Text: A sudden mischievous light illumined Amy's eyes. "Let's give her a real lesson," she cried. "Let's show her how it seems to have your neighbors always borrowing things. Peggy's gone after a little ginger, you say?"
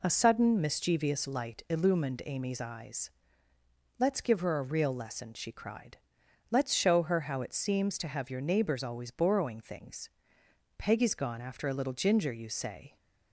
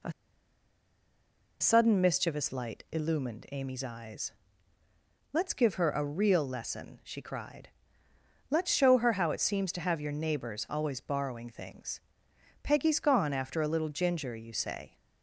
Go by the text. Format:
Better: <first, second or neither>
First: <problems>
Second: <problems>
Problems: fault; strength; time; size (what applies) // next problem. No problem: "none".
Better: first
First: none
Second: pauses between "A" and "sudden"; strong; at 0.1 s; 1.4 s long